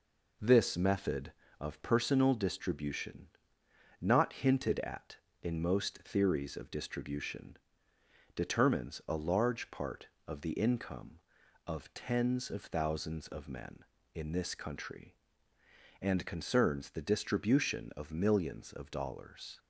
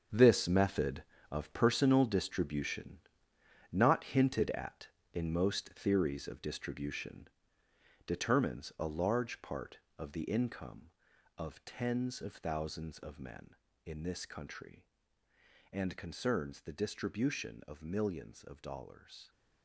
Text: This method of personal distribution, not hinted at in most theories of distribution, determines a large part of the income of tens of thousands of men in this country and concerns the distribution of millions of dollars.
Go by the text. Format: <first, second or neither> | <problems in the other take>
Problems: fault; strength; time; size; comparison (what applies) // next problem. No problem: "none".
first | gets quieter; strong; throughout; 11.5 dB